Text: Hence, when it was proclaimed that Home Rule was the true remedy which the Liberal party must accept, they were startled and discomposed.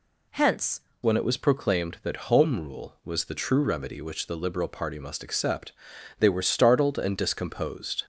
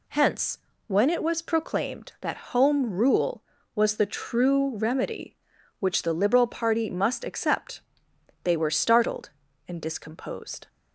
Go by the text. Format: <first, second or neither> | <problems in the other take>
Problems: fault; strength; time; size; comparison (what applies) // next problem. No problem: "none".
second | changes voice at "when"; from 1.0 s on; 7.0 s long